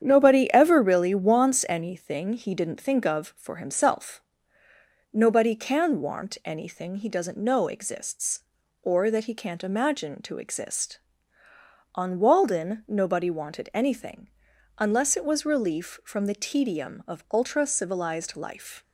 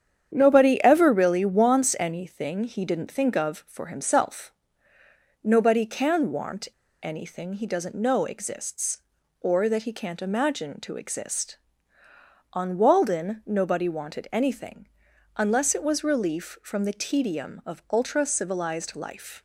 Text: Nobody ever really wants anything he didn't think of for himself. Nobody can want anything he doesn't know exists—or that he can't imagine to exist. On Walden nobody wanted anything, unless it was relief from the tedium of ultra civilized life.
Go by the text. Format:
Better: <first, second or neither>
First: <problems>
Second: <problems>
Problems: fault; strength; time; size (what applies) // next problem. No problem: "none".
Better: first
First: starts louder than the rest; strong; until 1.0 s; 8.5 dB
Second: starts louder than the rest; strong; until 1.3 s; 8.5 dB // pauses between "want" and "anything"; slight; at 6.6 s; 0.33 s long